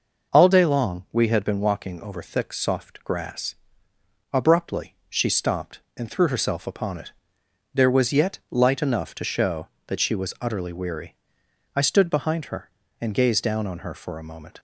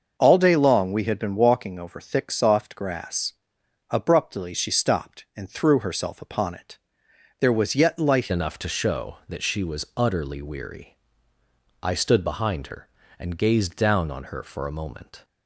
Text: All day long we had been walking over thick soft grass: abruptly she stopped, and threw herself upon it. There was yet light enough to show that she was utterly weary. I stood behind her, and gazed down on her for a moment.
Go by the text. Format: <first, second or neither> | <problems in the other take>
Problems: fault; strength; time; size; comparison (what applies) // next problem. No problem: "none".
first | starts louder than the rest; until 1.1 s; 6 dB // changes voice at "enough"; from 8.3 s on; 6.9 s long